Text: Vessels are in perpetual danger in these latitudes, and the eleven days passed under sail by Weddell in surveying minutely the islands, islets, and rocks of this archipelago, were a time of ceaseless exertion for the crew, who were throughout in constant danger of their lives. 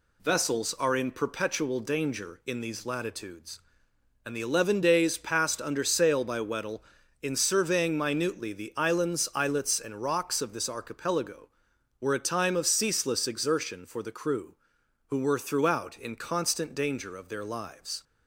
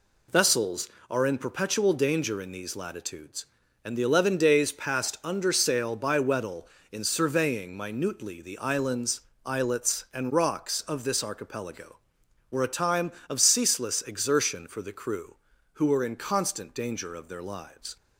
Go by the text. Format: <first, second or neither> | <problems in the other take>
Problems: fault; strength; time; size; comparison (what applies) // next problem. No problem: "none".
first | skips "throughout"; at 16.0 s